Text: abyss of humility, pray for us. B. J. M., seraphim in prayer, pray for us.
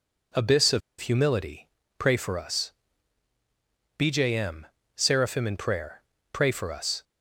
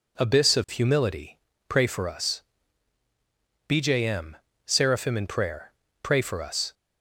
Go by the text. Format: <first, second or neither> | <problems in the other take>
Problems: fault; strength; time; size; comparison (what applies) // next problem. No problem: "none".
second | pauses between "of" and "humility"; slight; at 0.8 s; 0.20 s long